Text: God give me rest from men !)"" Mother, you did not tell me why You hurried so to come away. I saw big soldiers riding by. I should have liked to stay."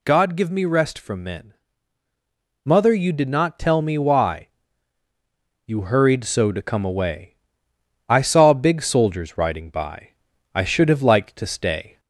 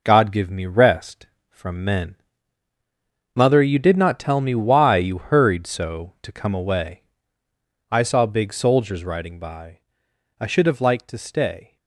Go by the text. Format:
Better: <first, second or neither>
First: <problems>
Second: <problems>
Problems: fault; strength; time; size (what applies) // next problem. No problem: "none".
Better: second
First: gets louder; strong; throughout; 8 dB // pauses between "why" and "You"; at 4.4 s; 1.2 s long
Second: none